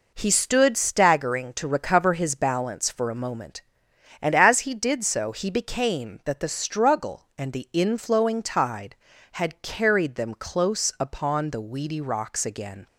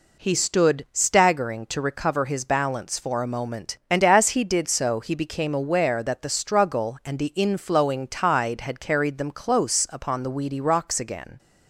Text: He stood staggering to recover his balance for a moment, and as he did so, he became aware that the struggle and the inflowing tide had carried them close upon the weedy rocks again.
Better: second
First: skips "aware"; at 6.2 s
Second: none

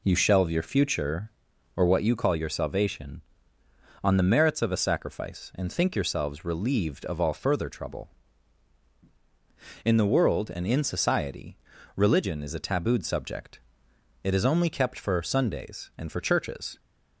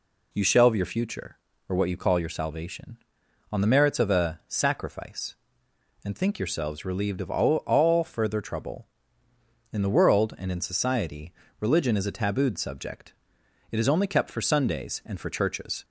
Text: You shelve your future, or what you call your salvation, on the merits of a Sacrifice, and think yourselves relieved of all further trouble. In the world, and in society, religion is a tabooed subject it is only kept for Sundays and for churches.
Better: first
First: pauses between "subject" and "it"; noticeable; at 13.6 s; 0.64 s long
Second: says "all" twice; at 7.5 s // pauses between "subject" and "it"; noticeable; at 13.1 s; 0.58 s long

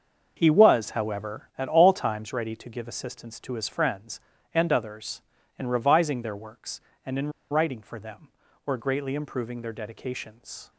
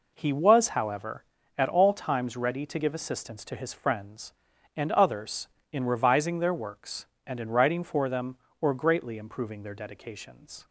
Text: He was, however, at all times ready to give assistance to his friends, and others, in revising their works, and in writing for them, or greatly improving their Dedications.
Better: second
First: starts louder than the rest; until 1.3 s; 6.5 dB // pauses between "in" and "writing"; slight; at 7.2 s; 0.21 s long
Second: none

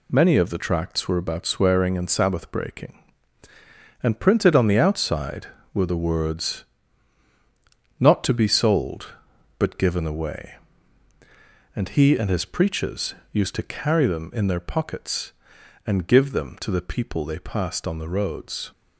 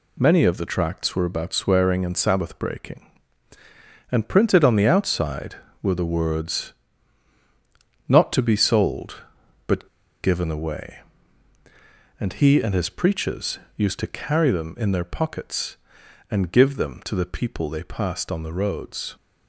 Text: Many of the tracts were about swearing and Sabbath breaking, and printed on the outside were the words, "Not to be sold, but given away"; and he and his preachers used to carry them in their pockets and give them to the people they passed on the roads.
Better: first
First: pauses between "preachers" and "used"; slight; at 13.1 s; 0.20 s long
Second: pauses between "but" and "given"; at 9.8 s; 0.36 s long // pauses between "preachers" and "used"; slight; at 13.5 s; 0.20 s long

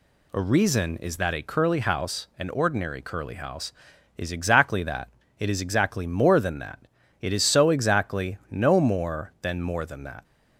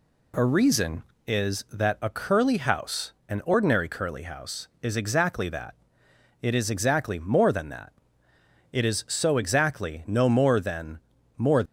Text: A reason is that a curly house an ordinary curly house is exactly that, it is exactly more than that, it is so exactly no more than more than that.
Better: first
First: none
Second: pauses between "house" and "an"; slight; at 3.1 s; 0.16 s long // pauses between "than" and "more"; at 10.9 s; 0.38 s long // stops before "than that"; at 11.6 s

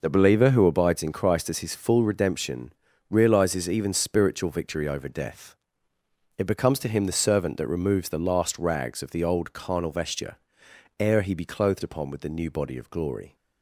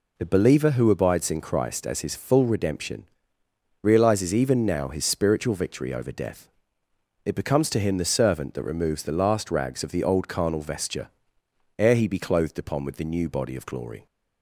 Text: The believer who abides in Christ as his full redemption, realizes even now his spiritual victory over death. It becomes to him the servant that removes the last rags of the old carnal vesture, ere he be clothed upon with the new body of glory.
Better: second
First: skips "now his"; at 3.9 s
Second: none

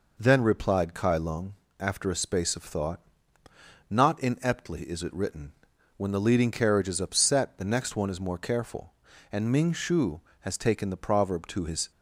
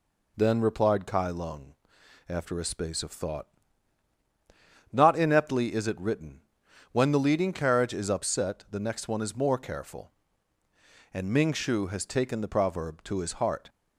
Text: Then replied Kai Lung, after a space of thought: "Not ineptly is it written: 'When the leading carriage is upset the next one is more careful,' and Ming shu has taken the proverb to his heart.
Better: second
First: stops before "heart"; at 11.9 s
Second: none

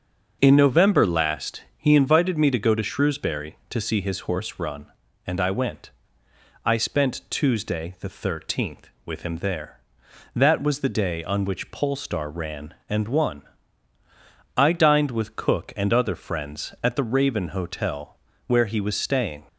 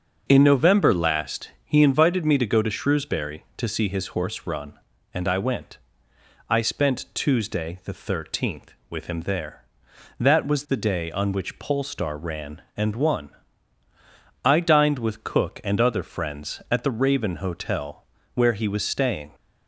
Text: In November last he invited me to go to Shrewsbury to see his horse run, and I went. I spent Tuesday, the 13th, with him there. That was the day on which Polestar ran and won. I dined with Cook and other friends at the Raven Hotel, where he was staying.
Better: neither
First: starts louder than the rest; until 1.4 s; 6.5 dB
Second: starts louder than the rest; until 1.2 s; 6.5 dB

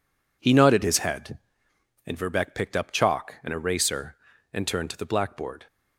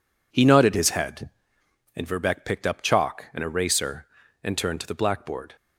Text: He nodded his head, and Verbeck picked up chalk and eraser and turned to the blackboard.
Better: neither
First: none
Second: none

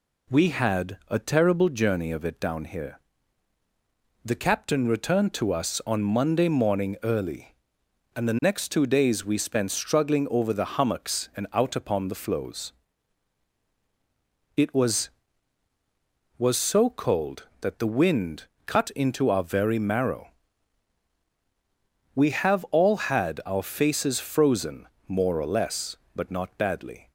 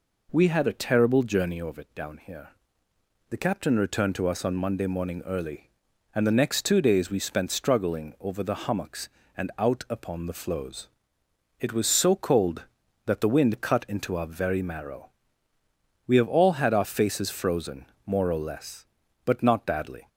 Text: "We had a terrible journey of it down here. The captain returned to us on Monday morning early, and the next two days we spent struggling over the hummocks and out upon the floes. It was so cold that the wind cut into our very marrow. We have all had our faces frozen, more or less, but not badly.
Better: second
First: says "was" twice; at 16.3 s // pauses between "wind" and "cut"; slight; at 18.4 s; 0.18 s long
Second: none

